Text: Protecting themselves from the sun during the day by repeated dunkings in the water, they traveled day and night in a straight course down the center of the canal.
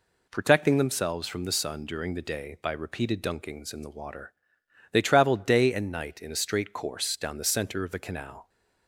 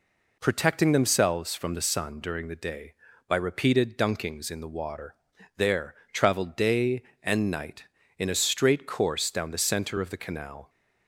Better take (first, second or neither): first